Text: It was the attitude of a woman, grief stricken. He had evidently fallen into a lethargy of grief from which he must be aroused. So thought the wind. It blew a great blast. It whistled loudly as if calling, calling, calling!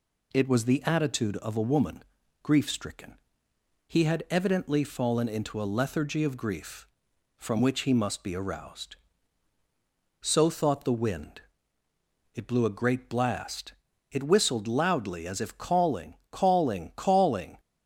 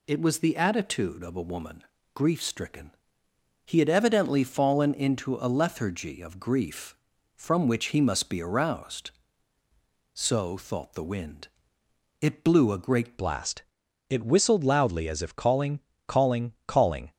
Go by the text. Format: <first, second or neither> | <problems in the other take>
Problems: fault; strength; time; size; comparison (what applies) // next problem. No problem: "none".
first | changes voice at "blast"; from 13.1 s on; 4.0 s long